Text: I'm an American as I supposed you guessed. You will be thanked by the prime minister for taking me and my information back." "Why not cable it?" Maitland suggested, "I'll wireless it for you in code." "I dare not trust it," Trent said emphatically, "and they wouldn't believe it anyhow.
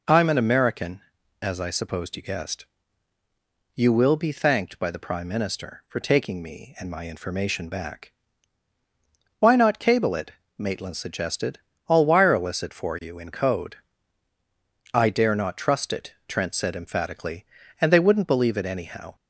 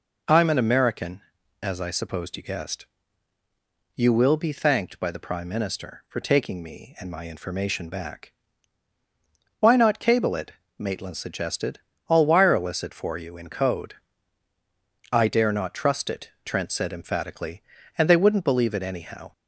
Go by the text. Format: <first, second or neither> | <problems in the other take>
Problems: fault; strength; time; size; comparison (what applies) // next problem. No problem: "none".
neither | none